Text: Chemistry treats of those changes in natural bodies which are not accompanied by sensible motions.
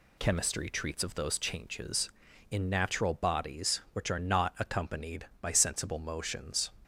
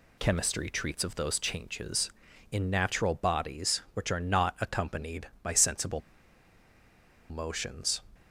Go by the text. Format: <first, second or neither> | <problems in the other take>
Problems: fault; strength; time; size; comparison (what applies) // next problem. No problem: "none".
first | pauses between "sensible" and "motions"; strong; at 6.0 s; 1.2 s long